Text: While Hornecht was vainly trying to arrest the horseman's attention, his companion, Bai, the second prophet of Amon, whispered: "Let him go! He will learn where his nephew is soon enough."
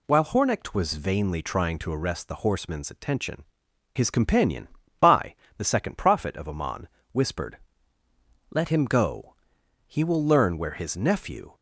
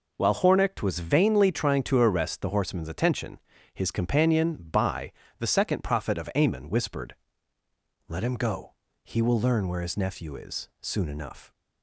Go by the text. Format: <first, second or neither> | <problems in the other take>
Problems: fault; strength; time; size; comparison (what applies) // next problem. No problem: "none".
second | stops before "is soon enough"; at 11.5 s